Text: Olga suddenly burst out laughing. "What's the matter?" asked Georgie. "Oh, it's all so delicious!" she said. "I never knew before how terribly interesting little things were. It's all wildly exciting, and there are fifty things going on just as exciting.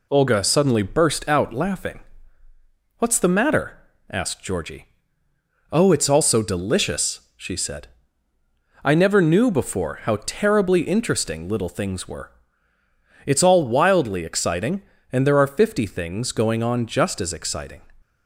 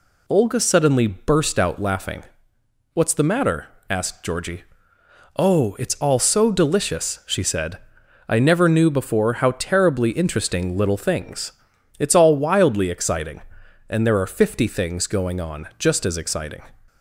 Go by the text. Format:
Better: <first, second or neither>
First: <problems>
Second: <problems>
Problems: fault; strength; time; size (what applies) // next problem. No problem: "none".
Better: first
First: none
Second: skips "were"; at 11.7 s